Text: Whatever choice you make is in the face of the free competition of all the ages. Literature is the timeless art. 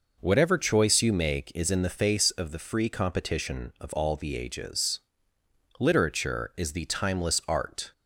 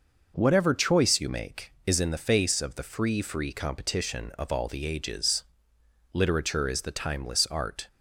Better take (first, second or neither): first